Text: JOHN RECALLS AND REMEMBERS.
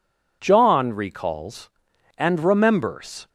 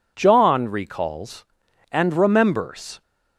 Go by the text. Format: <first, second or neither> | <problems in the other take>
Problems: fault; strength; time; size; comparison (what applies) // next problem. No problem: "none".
neither | none